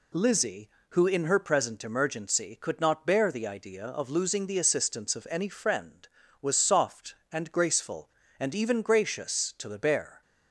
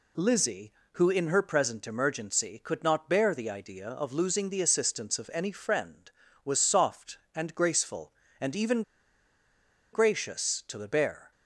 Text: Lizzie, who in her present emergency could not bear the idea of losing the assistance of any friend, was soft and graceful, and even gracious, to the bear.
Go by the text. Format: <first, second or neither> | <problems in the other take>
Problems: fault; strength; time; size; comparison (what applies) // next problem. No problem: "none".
first | pauses between "even" and "gracious"; at 8.8 s; 1.1 s long